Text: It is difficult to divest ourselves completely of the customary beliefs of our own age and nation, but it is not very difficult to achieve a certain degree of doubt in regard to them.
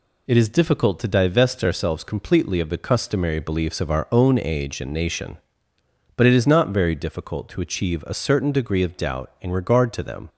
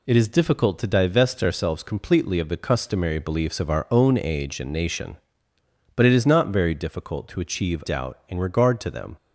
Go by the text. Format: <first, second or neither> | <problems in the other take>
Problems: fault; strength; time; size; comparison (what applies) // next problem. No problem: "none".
first | skips "a certain degree of"; at 7.8 s